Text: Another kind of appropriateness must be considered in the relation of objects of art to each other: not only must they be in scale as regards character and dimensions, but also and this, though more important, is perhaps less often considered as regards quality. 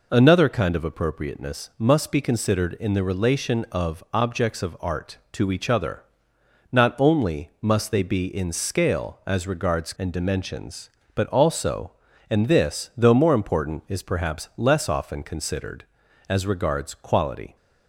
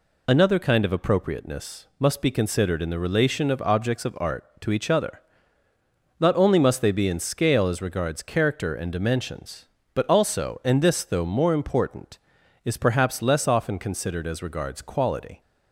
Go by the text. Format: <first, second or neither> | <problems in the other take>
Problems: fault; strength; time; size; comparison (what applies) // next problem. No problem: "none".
second | skips "character"; at 9.9 s